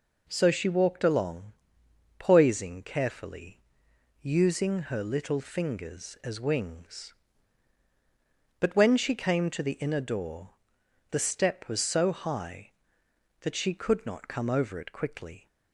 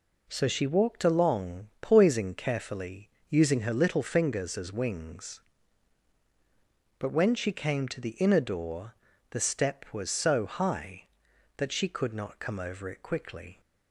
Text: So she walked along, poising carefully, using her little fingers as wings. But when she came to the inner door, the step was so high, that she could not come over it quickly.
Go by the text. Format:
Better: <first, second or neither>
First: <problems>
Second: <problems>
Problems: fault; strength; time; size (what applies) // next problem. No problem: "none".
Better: neither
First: none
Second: none